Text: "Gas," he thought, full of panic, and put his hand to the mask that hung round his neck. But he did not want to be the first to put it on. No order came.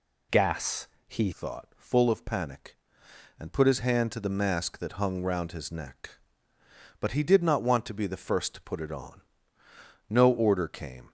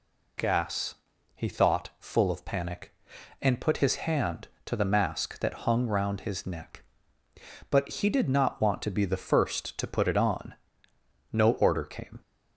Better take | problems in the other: second | changes voice at "thought"; from 1.3 s on; 9.8 s long

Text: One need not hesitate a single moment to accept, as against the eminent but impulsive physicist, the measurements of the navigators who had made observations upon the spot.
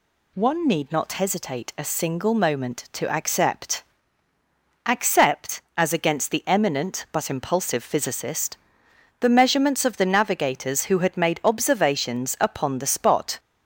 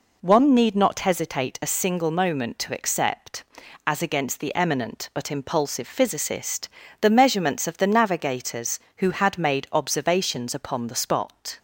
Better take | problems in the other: second | says "accept" twice; at 4.8 s

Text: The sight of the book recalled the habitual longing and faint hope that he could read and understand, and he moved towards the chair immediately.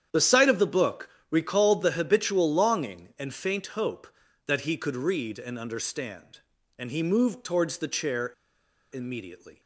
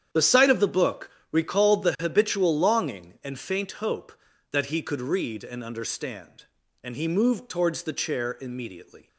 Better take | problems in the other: second | starts louder than the rest; strong; until 1.3 s; 9 dB; strong in the second // pauses between "book" and "recalled"; slight; at 1.1 s; 0.20 s long; slight in the second // pauses between "chair" and "immediately"; noticeable; at 8.3 s; 0.61 s long

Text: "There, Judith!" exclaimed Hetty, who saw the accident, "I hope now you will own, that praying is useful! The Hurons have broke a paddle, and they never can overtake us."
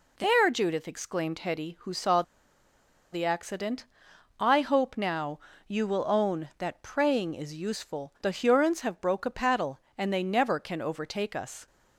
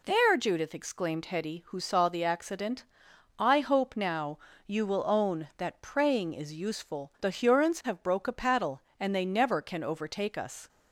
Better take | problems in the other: second | pauses between "saw" and "the"; noticeable; at 2.2 s; 0.89 s long // pauses between "now" and "you"; slight; at 5.4 s; 0.26 s long; slight in the second

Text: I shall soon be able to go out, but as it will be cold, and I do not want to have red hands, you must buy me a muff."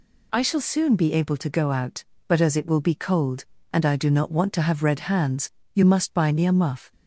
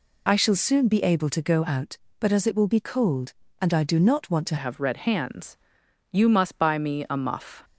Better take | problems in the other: first | changes voice at "have"; from 4.5 s on; 3.1 s long

